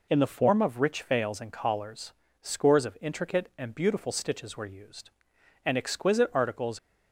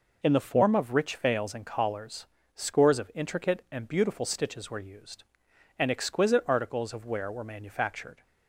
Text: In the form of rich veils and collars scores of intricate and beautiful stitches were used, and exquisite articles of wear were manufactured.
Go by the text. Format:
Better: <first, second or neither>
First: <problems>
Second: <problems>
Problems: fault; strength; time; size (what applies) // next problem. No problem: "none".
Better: second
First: pauses between "collars" and "scores"; slight; at 2.1 s; 0.30 s long // stops before "of wear were manufactured"; at 6.7 s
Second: pauses between "collars" and "scores"; slight; at 2.2 s; 0.30 s long